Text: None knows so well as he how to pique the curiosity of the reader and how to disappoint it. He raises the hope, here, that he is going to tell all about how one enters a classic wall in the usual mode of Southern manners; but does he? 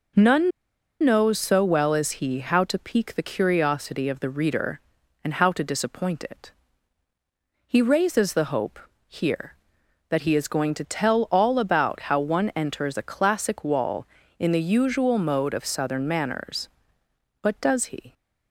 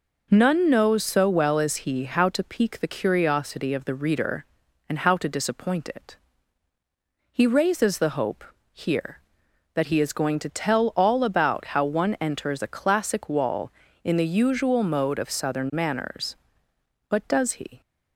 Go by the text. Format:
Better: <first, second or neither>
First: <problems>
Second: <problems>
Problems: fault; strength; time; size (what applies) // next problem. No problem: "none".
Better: second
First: pauses between "None" and "knows"; noticeable; at 0.5 s; 0.52 s long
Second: none